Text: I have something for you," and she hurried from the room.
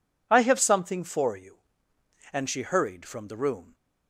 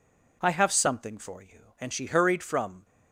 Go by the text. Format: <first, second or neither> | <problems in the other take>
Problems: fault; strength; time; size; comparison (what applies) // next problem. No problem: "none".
first | stops before "the room"; at 2.8 s